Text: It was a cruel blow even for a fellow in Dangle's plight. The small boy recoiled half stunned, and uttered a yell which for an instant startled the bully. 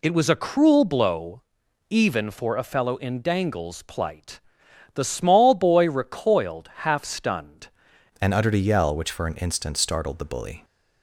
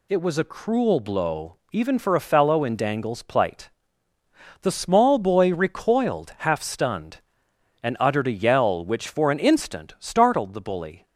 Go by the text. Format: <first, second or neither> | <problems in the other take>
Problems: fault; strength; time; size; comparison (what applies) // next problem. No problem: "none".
second | pauses between "blow" and "even"; noticeable; at 1.4 s; 0.48 s long; slight in the second // changes voice at "and"; from 8.2 s on; 2.4 s long